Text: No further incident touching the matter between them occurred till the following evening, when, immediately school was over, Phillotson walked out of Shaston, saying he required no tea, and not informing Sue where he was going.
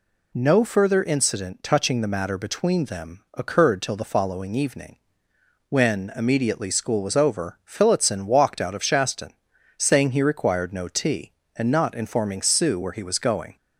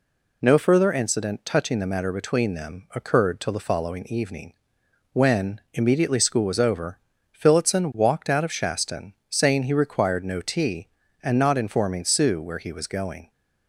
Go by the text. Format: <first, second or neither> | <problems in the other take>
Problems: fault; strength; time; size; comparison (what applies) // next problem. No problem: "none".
neither | none